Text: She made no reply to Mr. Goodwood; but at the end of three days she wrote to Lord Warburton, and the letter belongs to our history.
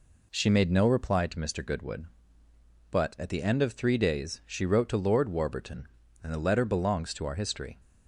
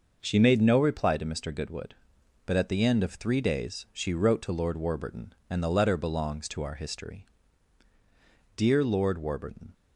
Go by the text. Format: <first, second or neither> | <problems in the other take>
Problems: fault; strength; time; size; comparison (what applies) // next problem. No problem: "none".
first | goes on to say "DEAR LORD WARBURTON"; noticeable; from 8.5 s on; 1.1 s long